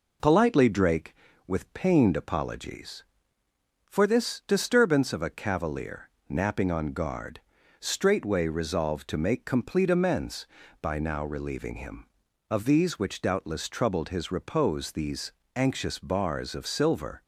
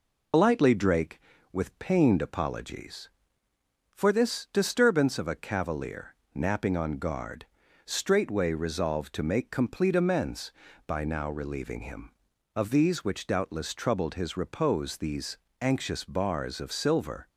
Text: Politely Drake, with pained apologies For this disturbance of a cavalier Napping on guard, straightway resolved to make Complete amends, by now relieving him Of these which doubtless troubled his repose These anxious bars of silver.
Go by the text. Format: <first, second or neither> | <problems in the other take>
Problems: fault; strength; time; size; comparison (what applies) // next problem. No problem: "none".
first | loses the start of "Politely"; at 0.3 s; 75 ms // pauses between "cavalier" and "Napping"; slight; at 6.1 s; 0.20 s long; slight in the first // pauses between "These" and "anxious"; slight; at 15.3 s; 0.24 s long; slight in the first